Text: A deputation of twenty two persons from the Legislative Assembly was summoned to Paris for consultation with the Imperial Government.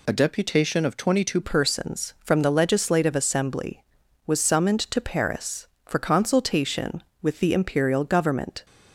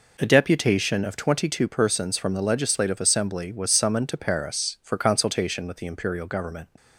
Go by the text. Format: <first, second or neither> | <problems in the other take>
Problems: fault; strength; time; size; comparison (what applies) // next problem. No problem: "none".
second | changes voice at "persons"; from 1.4 s on; 7.2 s long